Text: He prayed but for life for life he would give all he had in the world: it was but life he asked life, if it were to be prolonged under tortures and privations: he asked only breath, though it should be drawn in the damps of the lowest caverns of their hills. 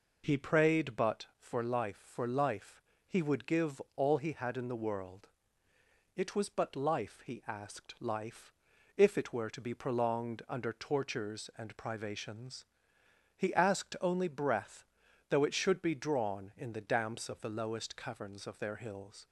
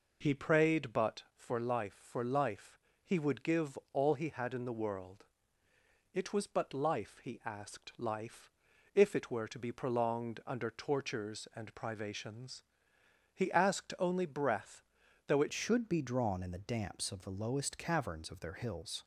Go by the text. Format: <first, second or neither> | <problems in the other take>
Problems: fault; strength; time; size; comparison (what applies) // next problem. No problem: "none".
first | pauses between "life" and "he"; slight; at 2.7 s; 0.26 s long; slight in the first // pauses between "give" and "all"; slight; at 3.7 s; 0.16 s long; slight in the first // changes voice at "should"; from 15.5 s on; 3.5 s long